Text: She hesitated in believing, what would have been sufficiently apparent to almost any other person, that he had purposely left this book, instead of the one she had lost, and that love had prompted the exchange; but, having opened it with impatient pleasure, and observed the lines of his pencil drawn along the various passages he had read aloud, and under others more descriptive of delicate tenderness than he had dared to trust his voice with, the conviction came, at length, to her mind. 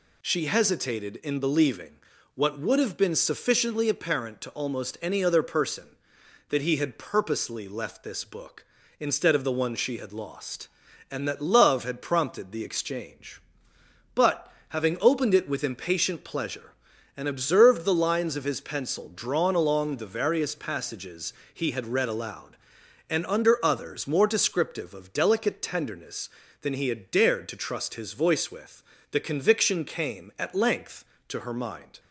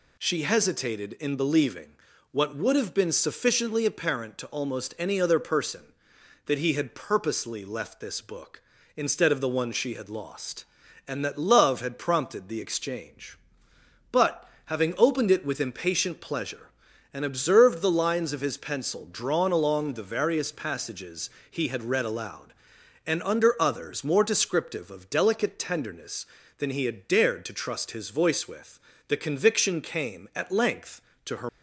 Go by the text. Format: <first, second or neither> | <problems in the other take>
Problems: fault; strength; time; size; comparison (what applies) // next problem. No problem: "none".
first | pauses between "passages" and "he"; slight; at 21.3 s; 0.18 s long; slight in the first // stops before "mind"; at 31.4 s